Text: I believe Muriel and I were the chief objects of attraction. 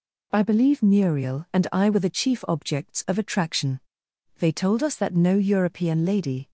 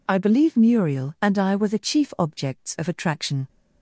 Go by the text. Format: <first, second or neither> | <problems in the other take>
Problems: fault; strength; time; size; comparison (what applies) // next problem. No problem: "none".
second | goes on to say "They told us that no European lady"; strong; from 4.3 s on; 2.1 s long